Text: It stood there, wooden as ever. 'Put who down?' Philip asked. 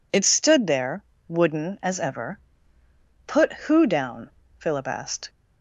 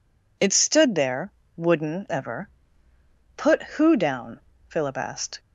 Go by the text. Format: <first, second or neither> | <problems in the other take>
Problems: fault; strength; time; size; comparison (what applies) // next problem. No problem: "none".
first | skips "as"; at 2.0 s